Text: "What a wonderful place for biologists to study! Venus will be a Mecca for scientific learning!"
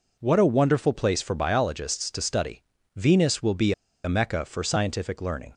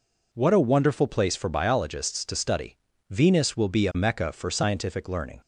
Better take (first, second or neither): second